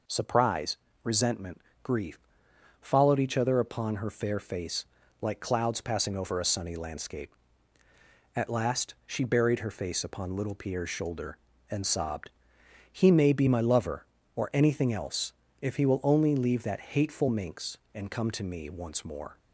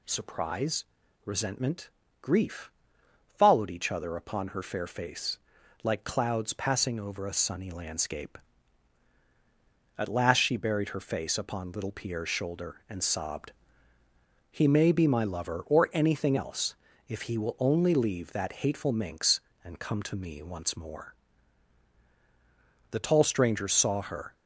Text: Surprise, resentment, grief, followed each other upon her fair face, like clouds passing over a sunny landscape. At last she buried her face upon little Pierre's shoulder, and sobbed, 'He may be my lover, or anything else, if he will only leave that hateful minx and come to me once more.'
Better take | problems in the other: first | goes on to say "The tall stranger saw her"; from 22.9 s on; 1.4 s long

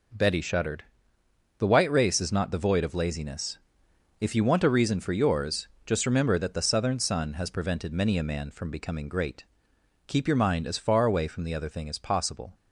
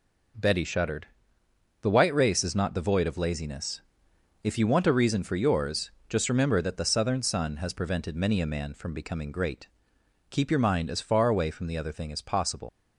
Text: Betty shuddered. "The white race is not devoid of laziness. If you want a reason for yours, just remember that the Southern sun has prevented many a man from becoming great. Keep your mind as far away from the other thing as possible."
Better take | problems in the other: first | leaves "possible" unfinished; at 12.6 s; 80 ms

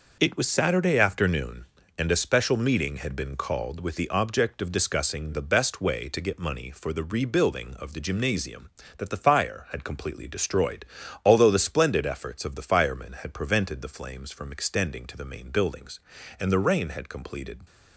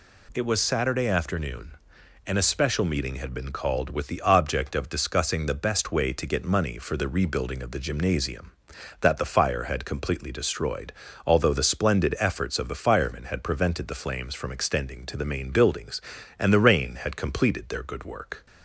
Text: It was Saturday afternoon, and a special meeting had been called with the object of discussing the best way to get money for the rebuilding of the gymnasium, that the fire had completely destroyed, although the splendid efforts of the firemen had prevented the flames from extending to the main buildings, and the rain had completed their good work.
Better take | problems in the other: second | stops before "their good work"; at 17.6 s

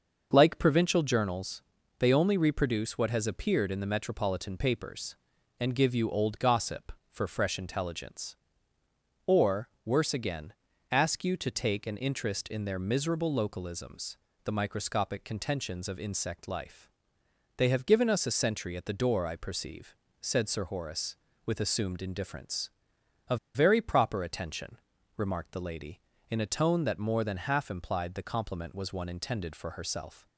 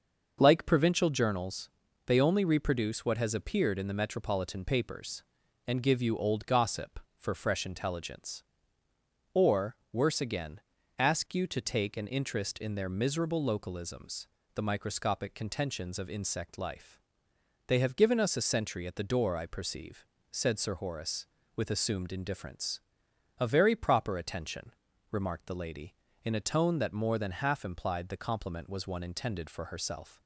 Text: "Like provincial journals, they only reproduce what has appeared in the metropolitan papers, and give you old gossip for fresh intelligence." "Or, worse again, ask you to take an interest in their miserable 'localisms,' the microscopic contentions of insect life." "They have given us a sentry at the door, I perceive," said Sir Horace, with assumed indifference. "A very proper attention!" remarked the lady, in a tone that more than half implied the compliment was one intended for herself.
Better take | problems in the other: second | starts louder than the rest; until 1.3 s; 6.5 dB; also in the second // pauses between "A" and "very"; slight; at 23.3 s; 0.18 s long

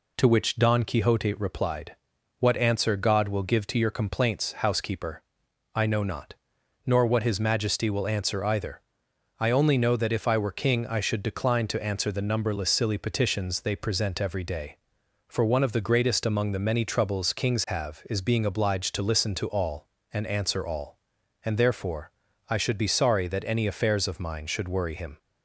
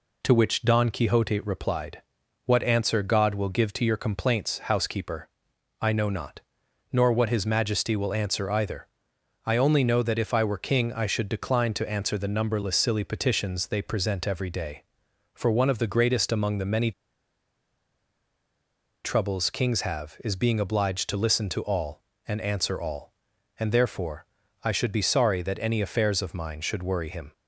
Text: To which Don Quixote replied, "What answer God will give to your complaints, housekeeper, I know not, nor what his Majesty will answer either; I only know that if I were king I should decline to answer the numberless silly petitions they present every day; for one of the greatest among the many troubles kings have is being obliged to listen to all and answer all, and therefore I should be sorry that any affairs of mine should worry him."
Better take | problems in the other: first | pauses between "many" and "troubles"; strong; at 16.9 s; 2.1 s long // pauses between "therefore" and "I"; at 24.2 s; 0.38 s long; also in the first

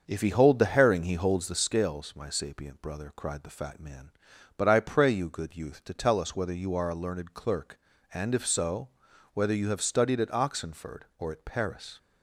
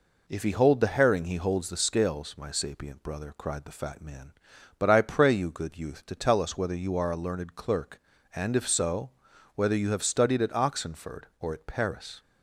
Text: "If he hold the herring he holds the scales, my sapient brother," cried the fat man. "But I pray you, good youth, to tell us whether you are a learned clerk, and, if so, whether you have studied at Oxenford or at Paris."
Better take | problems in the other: second | starts louder than the rest; until 1.6 s; 6.5 dB

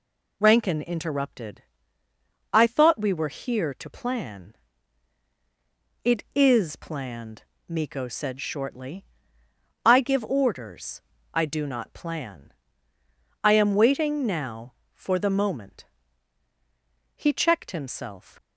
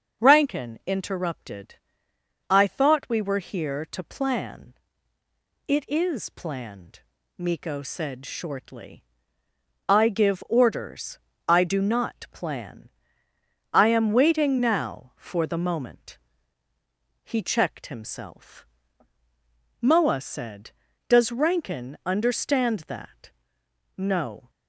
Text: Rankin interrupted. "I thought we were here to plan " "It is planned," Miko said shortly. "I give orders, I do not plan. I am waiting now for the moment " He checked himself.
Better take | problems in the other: first | starts louder than the rest; until 1.2 s; 7 dB // goes on to say "Moa said Does Rankin understand that no"; strong; from 19.8 s on; 4.6 s long

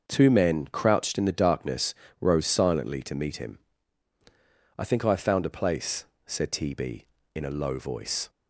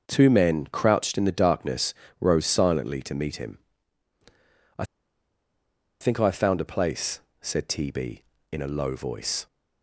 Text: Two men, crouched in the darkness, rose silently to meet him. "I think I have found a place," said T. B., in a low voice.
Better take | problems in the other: first | starts louder than the rest; until 1.0 s; 6.5 dB; also in the first // pauses between "I" and "think"; at 4.8 s; 1.1 s long

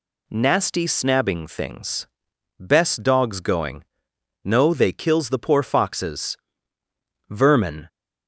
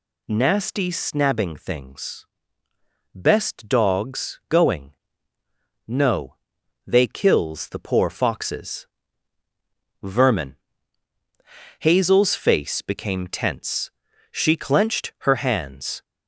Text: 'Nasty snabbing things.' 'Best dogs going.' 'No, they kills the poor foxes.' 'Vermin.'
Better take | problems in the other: first | goes on to say "Hazel's face became tense She clenched her hands"; strong; from 11.7 s on; 4.2 s long

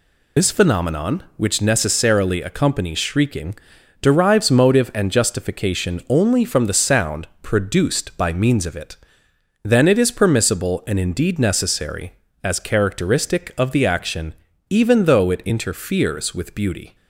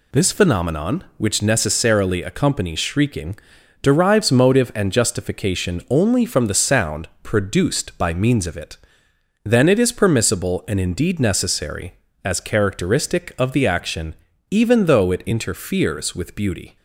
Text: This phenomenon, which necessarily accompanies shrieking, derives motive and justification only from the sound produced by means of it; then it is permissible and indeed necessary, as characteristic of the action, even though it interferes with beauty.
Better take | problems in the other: second | loses the start of "This"; at 0.3 s; 55 ms // pauses between "sound" and "produced"; slight; at 7.2 s; 0.16 s long; slight in the second

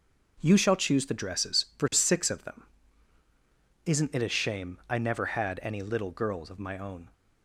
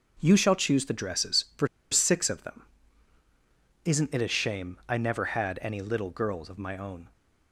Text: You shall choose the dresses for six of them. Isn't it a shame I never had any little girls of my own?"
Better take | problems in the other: first | pauses between "for" and "six"; slight; at 1.6 s; 0.24 s long

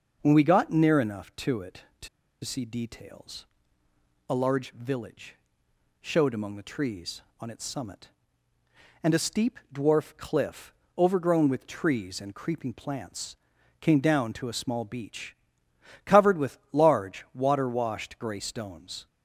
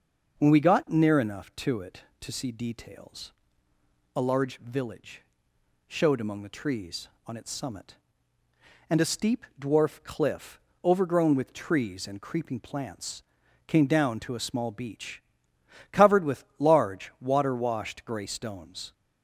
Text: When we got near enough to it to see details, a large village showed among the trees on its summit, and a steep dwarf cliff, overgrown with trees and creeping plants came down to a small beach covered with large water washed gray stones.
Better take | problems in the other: second | starts louder than the rest; noticeable; until 1.2 s; 6 dB; noticeable in the second // pauses between "to" and "see"; slight; at 2.0 s; 0.35 s long // pauses between "village" and "showed"; noticeable; at 5.3 s; 0.66 s long; noticeable in the second // pauses between "plants" and "came"; at 13.3 s; 0.44 s long; also in the second // pauses between "beach" and "covered"; noticeable; at 15.3 s; 0.70 s long; noticeable in the second

